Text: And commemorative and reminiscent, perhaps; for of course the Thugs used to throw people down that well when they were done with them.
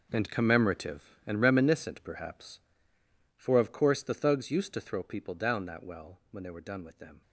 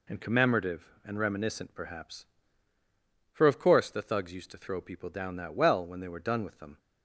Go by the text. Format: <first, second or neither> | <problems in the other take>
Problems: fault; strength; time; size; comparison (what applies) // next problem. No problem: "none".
second | gets quieter; strong; throughout; 13 dB